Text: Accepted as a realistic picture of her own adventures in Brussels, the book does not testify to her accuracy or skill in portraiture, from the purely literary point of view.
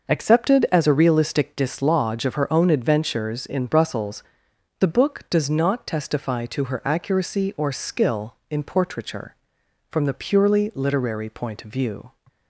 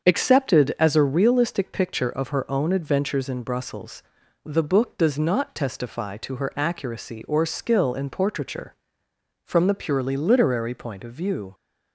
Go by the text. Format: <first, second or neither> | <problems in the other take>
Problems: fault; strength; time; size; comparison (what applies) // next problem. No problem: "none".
second | starts louder than the rest; noticeable; until 1.1 s; 6 dB; also in the second // says "dislodge" for "picture"; at 1.5 s